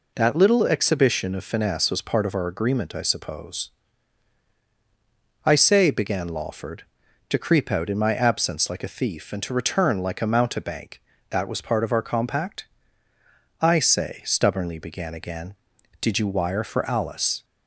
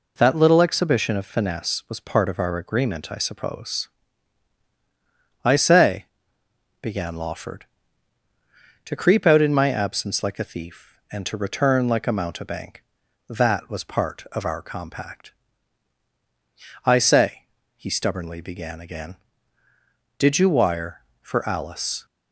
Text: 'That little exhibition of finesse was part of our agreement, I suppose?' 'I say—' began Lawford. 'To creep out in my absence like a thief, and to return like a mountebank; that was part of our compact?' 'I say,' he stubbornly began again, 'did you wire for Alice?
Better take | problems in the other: second | skips "he"; at 14.2 s

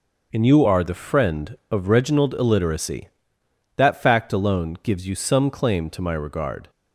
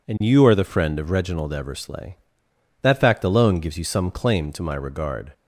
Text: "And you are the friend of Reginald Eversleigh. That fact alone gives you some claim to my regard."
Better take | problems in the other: second | starts louder than the rest; until 1.3 s; 6 dB // says "Illiteracy" for "Eversleigh"; at 2.3 s

